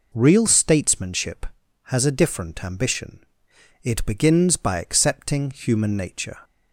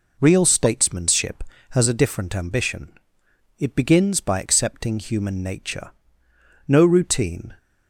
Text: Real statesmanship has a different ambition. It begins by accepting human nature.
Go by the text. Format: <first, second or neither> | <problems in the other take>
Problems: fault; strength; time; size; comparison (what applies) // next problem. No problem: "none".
first | goes on to say "No routine"; noticeable; from 6.6 s on; 0.90 s long